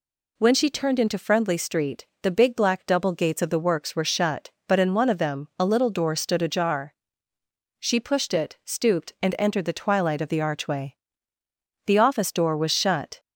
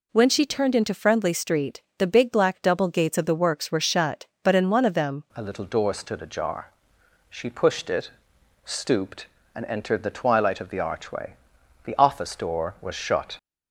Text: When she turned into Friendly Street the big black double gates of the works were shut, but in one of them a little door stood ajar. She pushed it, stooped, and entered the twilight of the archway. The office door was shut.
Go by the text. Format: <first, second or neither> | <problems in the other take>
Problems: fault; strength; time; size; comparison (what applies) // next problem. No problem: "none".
first | pauses between "Street" and "the"; slight; at 1.8 s; 0.16 s long; slight in the first // changes voice at "a"; from 5.3 s on; 8.0 s long